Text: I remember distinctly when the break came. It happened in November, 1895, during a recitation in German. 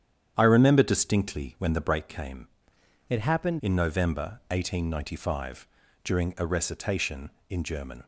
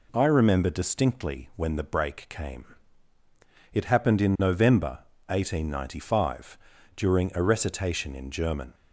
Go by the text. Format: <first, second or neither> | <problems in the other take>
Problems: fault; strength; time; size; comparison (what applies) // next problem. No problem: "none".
second | starts louder than the rest; strong; until 1.3 s; 9 dB // changes voice from "It" to "happened"; from 3.0 to 3.5 s; 0.5 s long